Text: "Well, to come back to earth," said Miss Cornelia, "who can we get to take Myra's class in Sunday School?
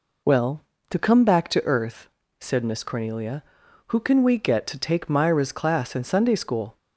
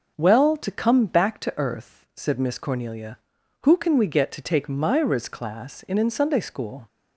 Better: first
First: none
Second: starts louder than the rest; until 1.1 s; 6.5 dB // says "in" twice; at 5.9 s

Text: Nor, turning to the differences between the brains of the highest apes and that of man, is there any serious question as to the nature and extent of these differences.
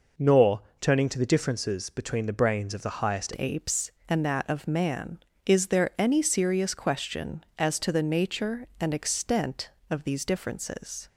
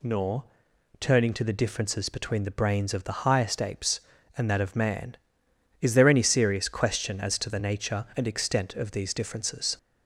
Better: second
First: changes voice at "apes"; from 3.3 s on; 7.7 s long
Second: none

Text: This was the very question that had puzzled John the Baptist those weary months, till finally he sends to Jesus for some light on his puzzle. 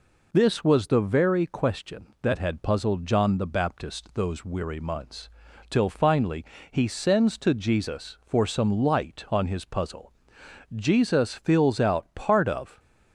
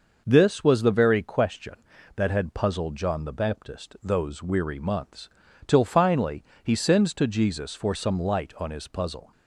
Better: second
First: pauses between "finally" and "he"; slight; at 6.4 s; 0.26 s long // goes on to say "Jesus fills out part of"; strong; from 10.7 s on; 2.0 s long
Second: pauses between "finally" and "he"; slight; at 6.4 s; 0.20 s long

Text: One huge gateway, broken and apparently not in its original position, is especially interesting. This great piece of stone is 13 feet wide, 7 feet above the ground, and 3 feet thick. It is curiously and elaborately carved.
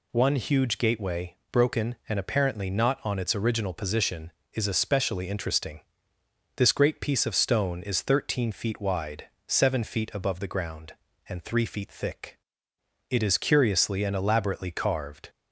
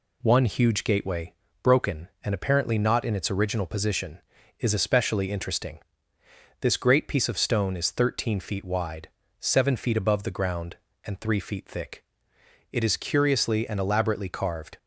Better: second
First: says "on" for "in"; at 3.0 s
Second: none

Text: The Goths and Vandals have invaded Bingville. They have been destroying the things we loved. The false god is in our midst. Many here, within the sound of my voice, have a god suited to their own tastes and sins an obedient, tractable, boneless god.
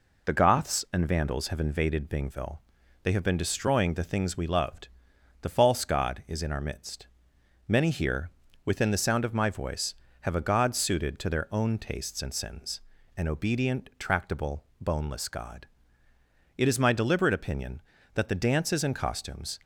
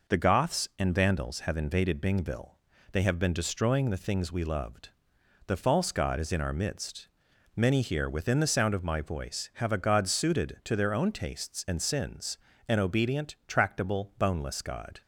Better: second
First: pauses between "sins" and "an"; slight; at 12.8 s; 0.36 s long // goes on to say "It is my deliberate opinion that the dances and costumes"; strong; from 16.5 s on; 3.0 s long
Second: pauses between "sins" and "an"; slight; at 12.3 s; 0.30 s long

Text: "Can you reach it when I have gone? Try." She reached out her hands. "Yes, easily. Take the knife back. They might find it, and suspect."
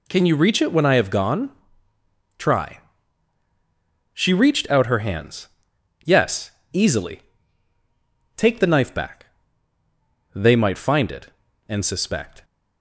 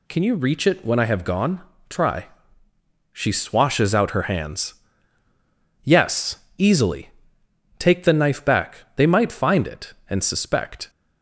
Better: first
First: none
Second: says "swashes" for "reached"; at 3.3 s

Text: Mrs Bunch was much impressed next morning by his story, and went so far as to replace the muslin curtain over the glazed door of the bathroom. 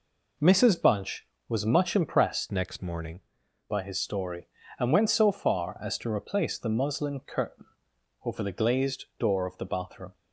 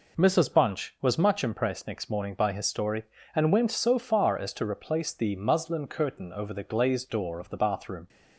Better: second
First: changes voice from "next" to "morning"; from 2.5 to 3.2 s; 0.7 s long // pauses between "curtain" and "over"; noticeable; at 7.6 s; 0.58 s long // pauses between "glazed" and "door"; slight; at 9.0 s; 0.16 s long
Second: none

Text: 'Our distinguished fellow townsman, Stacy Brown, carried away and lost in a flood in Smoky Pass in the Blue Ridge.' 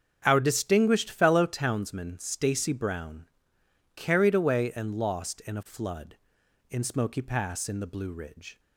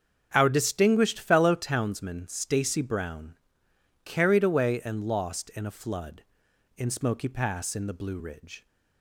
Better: neither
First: starts louder than the rest; strong; until 1.2 s; 7.5 dB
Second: starts louder than the rest; strong; until 1.3 s; 7.5 dB

